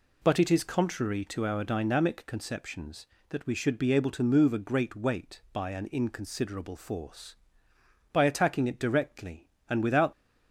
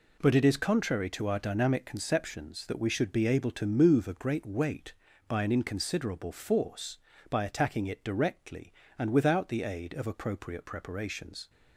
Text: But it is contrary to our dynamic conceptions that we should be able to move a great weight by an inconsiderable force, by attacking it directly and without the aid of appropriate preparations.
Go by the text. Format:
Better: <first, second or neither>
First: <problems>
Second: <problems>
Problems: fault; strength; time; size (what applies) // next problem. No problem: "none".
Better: second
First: stops before "the aid of appropriate preparations"; at 10.1 s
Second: none